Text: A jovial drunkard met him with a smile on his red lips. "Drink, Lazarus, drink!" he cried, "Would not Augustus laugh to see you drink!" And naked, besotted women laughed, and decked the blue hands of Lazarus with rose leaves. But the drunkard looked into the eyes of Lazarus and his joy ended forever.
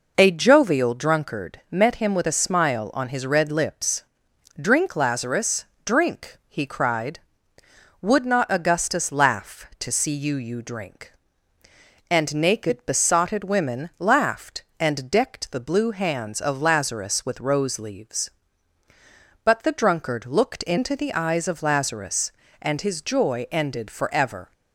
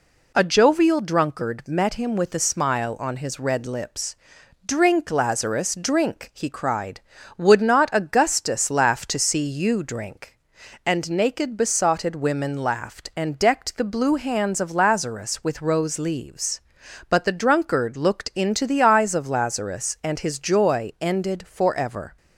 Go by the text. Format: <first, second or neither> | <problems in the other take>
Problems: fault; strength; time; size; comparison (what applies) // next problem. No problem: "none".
second | says "you" twice; at 10.3 s